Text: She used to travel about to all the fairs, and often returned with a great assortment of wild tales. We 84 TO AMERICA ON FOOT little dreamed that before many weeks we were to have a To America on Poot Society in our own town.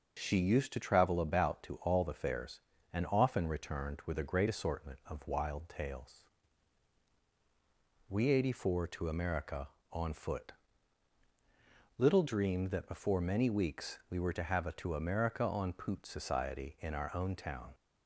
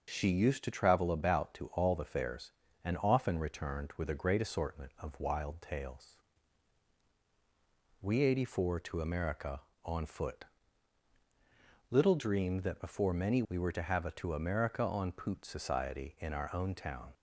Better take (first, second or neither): first